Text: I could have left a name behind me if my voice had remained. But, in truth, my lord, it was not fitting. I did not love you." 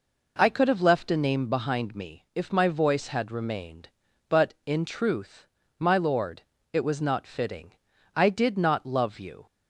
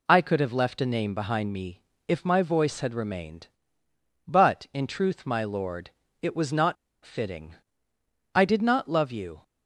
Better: first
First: none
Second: pauses between "me" and "if"; slight; at 1.8 s; 0.24 s long // pauses between "not" and "fitting"; slight; at 6.7 s; 0.29 s long

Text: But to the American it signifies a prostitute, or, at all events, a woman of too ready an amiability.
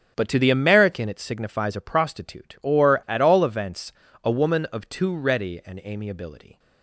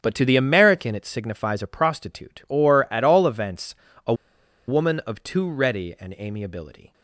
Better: first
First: starts louder than the rest; until 1.1 s; 7 dB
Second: starts louder than the rest; strong; until 1.0 s; 7 dB // pauses between "a" and "woman"; noticeable; at 4.1 s; 0.54 s long

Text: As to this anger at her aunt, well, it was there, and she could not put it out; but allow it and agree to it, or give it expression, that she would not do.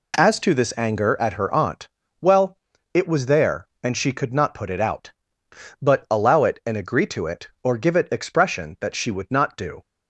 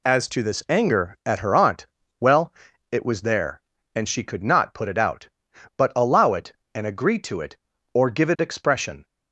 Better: first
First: none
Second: stops before "that she would not do"; at 9.0 s

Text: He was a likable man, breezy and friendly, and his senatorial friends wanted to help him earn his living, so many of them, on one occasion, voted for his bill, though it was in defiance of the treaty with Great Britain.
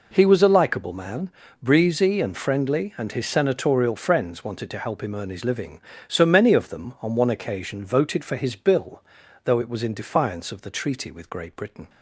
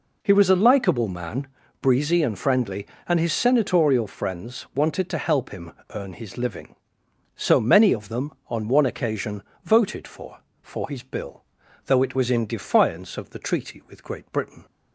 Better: first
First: none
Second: pauses between "him" and "earn"; slight; at 5.7 s; 0.22 s long // says "for" twice; at 10.6 s

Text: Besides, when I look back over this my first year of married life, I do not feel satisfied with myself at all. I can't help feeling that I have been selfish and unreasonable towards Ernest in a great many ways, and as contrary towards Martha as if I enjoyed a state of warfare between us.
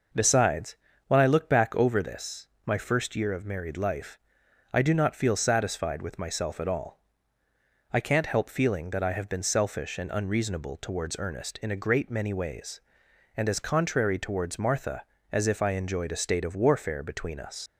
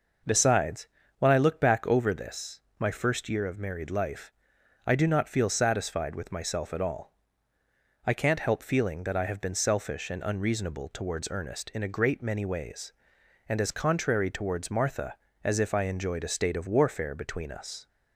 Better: second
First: pauses between "this" and "my"; slight; at 2.4 s; 0.18 s long // leaves "us" unfinished; at 17.6 s; 95 ms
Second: pauses between "this" and "my"; slight; at 2.6 s; 0.18 s long

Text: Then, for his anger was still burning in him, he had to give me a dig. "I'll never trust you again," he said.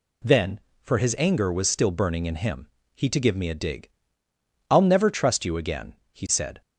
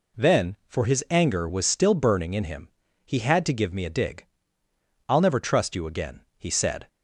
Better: second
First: skips "had"; at 3.0 s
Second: none

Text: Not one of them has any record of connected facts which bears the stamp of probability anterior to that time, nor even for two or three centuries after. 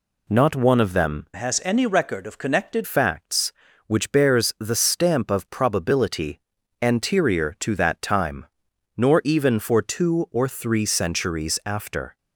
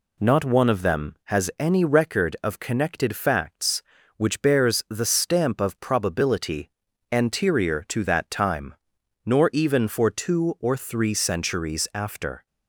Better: second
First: changes voice from "has" to "connected"; from 1.3 to 2.8 s; 1.5 s long // pauses between "probability" and "anterior"; at 6.4 s; 0.40 s long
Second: pauses between "probability" and "anterior"; at 6.7 s; 0.40 s long

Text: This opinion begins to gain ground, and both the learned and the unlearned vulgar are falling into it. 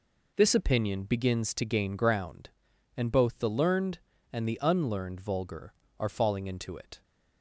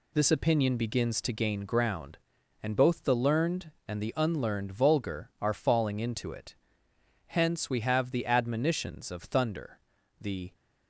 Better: first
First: none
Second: goes on to say "Hence we have the admonitions of thunder the"; strong; from 7.2 s on; 3.2 s long

